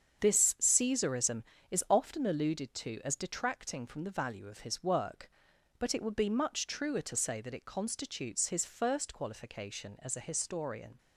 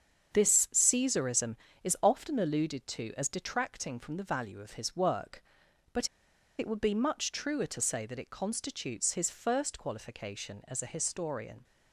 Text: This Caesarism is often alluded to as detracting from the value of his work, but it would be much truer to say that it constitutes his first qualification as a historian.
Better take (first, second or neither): first